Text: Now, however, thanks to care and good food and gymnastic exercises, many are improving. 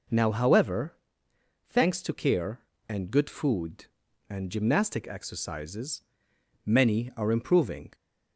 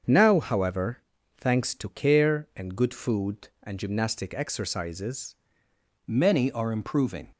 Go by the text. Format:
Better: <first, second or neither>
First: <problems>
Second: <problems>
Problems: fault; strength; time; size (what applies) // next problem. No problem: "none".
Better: first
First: none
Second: starts louder than the rest; until 1.4 s; 7 dB // changes voice at "many"; from 6.0 s on; 1.2 s long